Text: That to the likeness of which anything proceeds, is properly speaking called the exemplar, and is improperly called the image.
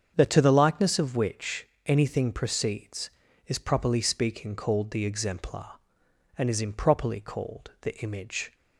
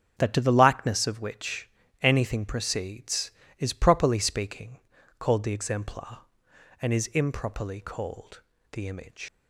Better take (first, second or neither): first